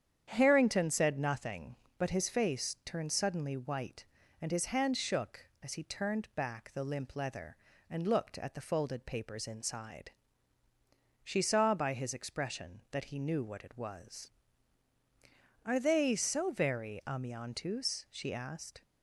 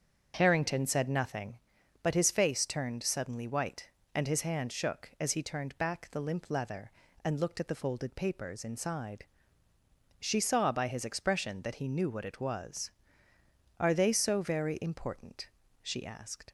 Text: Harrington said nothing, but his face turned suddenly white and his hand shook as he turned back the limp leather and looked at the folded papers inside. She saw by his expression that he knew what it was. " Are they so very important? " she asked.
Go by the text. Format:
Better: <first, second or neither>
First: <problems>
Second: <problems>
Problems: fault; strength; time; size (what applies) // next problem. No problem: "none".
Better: second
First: starts louder than the rest; strong; until 1.2 s; 8.5 dB // says "amiantus" for "important"; at 17.0 s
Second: starts louder than the rest; strong; until 1.3 s; 7 dB